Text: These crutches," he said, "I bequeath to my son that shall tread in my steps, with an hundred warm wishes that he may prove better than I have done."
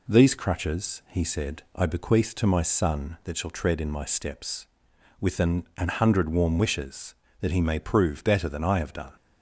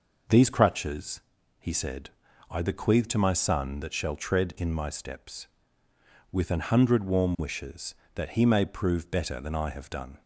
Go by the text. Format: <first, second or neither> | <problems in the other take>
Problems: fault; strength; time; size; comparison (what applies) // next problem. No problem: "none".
second | says "an" twice; at 5.7 s